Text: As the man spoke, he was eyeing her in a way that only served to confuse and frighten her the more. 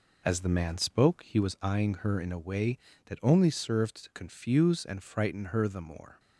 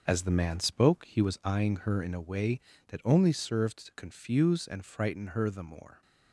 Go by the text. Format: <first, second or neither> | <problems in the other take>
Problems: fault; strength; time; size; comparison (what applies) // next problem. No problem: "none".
first | gets quieter; strong; throughout; 8.5 dB